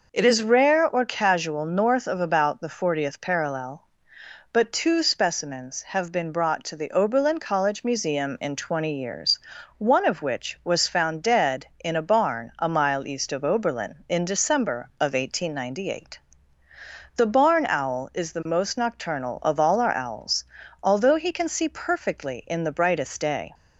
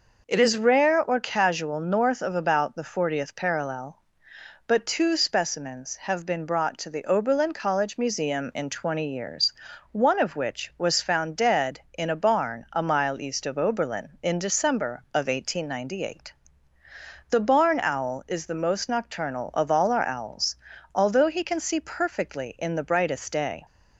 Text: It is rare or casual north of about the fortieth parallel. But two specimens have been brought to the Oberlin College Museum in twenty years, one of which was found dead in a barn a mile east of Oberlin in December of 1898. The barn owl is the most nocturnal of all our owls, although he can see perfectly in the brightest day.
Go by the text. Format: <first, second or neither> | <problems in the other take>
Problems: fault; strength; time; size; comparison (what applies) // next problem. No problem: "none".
neither | none